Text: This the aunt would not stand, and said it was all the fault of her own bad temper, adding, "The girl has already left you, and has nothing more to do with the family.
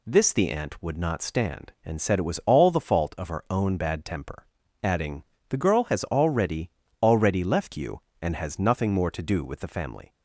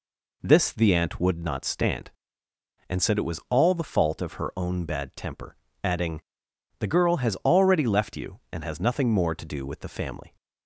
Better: second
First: says "already" twice; at 7.0 s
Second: none

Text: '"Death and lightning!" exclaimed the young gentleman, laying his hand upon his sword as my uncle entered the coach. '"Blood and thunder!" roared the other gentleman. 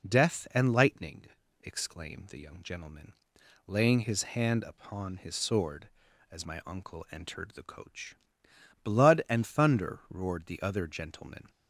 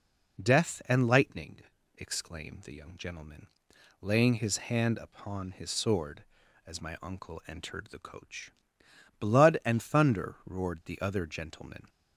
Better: neither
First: none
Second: none

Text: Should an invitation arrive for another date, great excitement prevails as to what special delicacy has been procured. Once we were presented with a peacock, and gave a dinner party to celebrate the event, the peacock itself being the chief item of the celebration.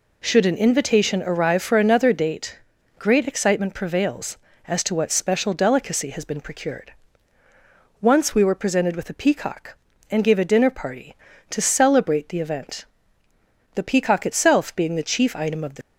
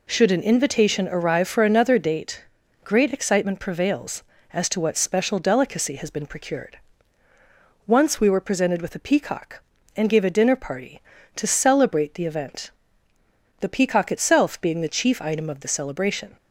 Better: second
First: stops before "celebration"; at 15.8 s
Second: none

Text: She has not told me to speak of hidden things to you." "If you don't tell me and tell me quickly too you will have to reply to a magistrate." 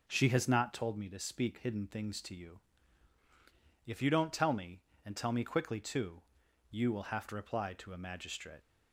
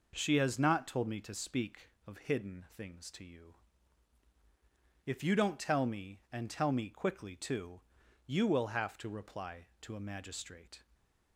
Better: second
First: skips "of"; at 1.5 s // pauses between "too" and "you"; noticeable; at 6.2 s; 0.48 s long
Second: pauses between "too" and "you"; noticeable; at 7.8 s; 0.46 s long

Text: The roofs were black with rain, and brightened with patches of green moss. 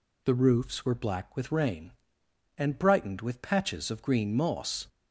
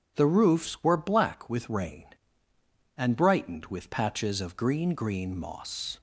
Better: first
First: none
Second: says "green" twice; at 4.9 s

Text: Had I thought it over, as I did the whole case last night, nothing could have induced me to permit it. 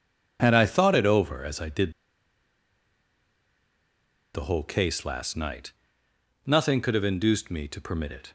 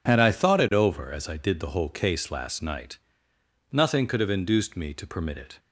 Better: second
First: pauses between "did" and "the"; strong; at 1.9 s; 2.4 s long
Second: none

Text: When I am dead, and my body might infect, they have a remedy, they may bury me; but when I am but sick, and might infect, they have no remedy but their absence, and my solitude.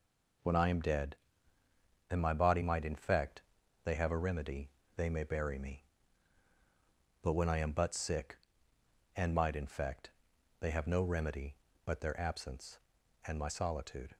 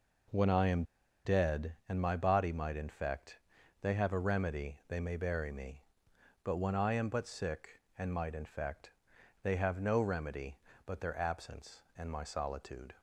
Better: first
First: none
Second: pauses between "am" and "dead"; at 0.8 s; 0.42 s long

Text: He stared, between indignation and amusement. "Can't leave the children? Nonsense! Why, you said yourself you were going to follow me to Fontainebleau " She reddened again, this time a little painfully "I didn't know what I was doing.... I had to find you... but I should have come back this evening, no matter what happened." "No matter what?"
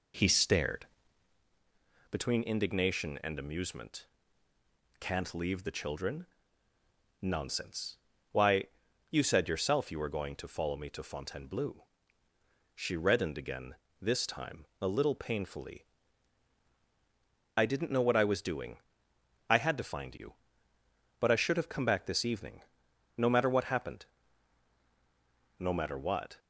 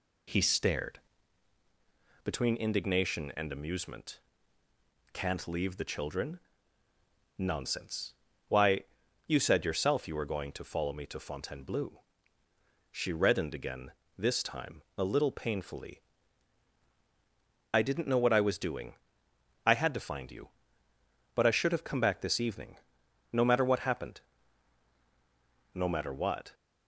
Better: second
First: starts louder than the rest; until 1.4 s; 3.5 dB // pauses between "time" and "a"; slight; at 14.6 s; 0.16 s long // pauses between "painfully" and "I"; strong; at 15.8 s; 1.7 s long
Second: pauses between "time" and "a"; slight; at 14.8 s; 0.16 s long // pauses between "painfully" and "I"; strong; at 15.9 s; 1.7 s long

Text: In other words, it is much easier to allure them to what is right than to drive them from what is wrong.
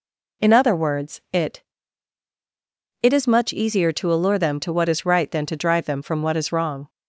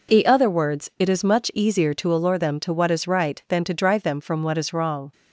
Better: second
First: says "it" twice; at 3.0 s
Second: none

